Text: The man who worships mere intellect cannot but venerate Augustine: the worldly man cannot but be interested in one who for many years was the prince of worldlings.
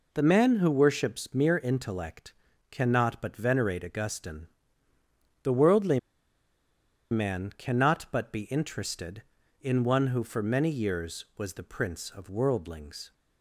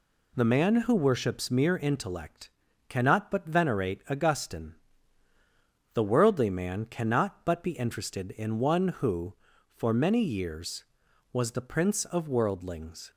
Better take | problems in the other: second | pauses between "intellect" and "cannot"; slight; at 2.3 s; 0.36 s long; also in the second // pauses between "worldly" and "man"; at 5.9 s; 1.1 s long

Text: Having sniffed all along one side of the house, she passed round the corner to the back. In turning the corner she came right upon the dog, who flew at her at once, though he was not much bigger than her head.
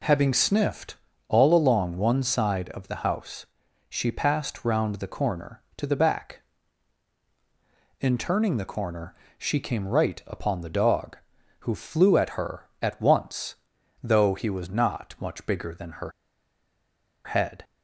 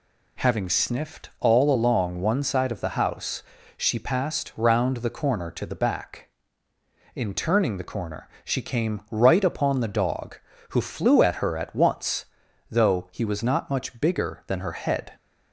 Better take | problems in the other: second | pauses between "sniffed" and "all"; slight; at 0.9 s; 0.32 s long // pauses between "corner" and "she"; slight; at 9.1 s; 0.24 s long; slight in the second // pauses between "her" and "head"; at 16.1 s; 1.1 s long

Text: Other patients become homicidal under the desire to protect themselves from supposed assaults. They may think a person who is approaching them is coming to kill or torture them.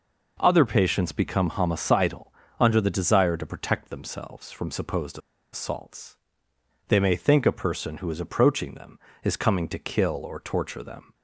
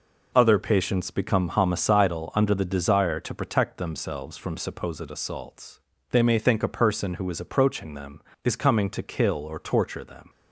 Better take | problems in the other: second | pauses between "homicidal" and "under"; slight; at 2.3 s; 0.28 s long // pauses between "supposed" and "assaults"; slight; at 5.1 s; 0.34 s long

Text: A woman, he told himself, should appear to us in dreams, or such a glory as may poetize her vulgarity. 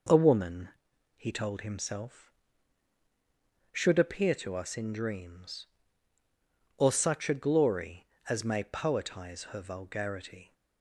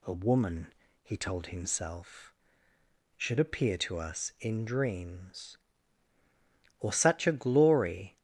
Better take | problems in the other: first | stops before "as may poetize her vulgarity"; at 8.1 s

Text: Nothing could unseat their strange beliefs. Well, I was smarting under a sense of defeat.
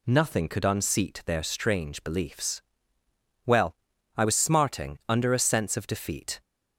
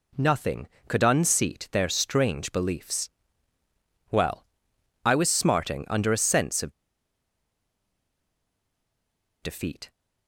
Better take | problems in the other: first | pauses between "of" and "defeat"; strong; at 6.7 s; 2.7 s long

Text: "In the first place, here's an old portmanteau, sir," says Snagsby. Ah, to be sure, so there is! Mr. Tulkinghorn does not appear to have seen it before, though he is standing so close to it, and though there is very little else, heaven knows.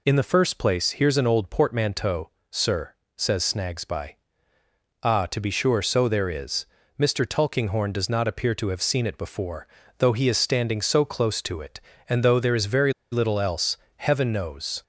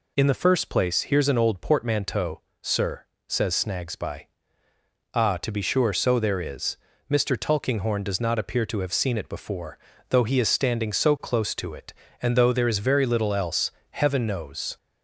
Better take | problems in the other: second | pauses between "very" and "little"; slight; at 12.9 s; 0.19 s long

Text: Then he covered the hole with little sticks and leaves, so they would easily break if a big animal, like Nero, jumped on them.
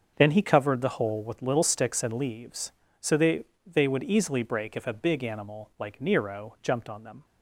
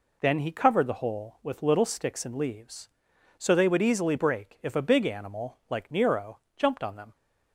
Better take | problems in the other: second | starts louder than the rest; until 1.1 s; 6.5 dB // says "they" twice; at 3.6 s

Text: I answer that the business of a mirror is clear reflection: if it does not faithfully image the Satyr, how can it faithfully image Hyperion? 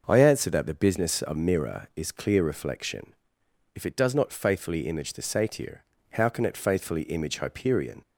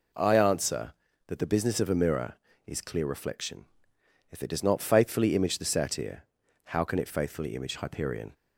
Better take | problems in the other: second | starts louder than the rest; until 1.0 s; 6 dB // skips "a"; at 1.3 s

